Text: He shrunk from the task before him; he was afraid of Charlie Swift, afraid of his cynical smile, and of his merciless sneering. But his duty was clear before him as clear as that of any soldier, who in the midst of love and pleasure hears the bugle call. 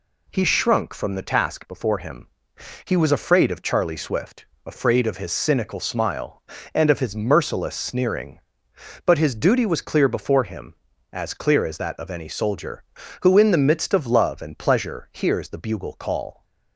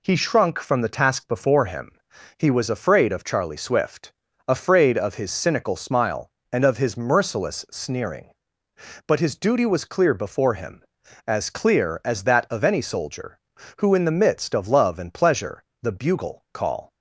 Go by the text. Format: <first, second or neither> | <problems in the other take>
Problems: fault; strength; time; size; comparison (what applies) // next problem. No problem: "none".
first | skips "hears"; at 15.7 s